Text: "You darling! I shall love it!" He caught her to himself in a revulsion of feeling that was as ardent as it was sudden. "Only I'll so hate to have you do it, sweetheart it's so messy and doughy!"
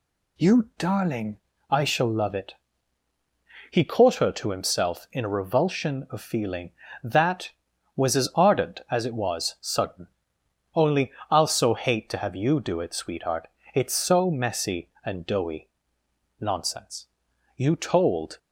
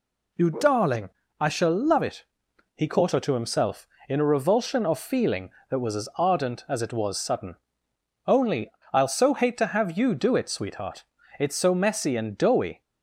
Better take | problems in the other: second | pauses between "Only" and "I'll"; slight; at 11.0 s; 0.20 s long; slight in the second // pauses between "sweetheart" and "it's"; slight; at 13.4 s; 0.24 s long; slight in the second // goes on to say "Nonsense You told"; strong; from 16.3 s on; 2.0 s long

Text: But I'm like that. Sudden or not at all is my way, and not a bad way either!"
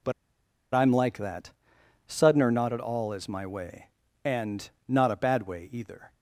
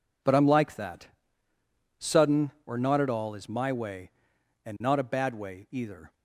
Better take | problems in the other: second | pauses between "But" and "I'm"; noticeable; at 0.1 s; 0.60 s long // pauses between "and" and "not"; slight; at 4.6 s; 0.20 s long

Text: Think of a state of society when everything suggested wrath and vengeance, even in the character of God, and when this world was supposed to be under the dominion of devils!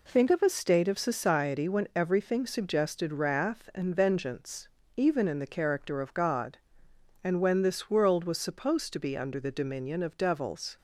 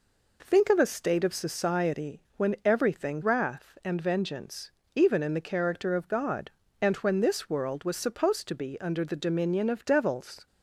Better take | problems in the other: first | skips "suggested"; at 3.2 s

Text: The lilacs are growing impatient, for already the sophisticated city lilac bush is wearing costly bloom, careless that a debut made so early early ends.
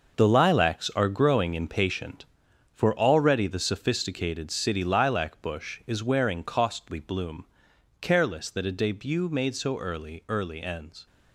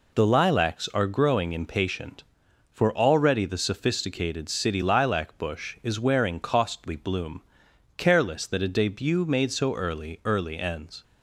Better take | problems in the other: second | gets quieter; strong; throughout; 10 dB

